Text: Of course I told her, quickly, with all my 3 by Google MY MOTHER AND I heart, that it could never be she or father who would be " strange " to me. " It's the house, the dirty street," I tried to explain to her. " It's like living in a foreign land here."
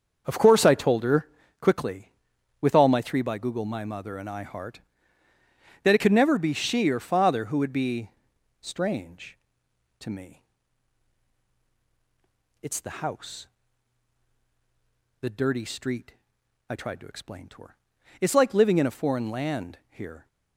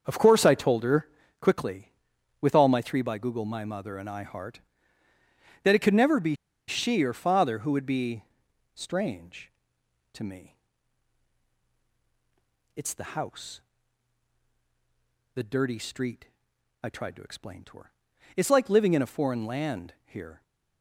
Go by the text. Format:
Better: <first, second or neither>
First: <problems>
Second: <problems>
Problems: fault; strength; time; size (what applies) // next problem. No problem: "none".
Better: first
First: starts louder than the rest; until 1.2 s; 7 dB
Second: starts louder than the rest; until 1.0 s; 7 dB // pauses between "be" and "she"; slight; at 6.3 s; 0.33 s long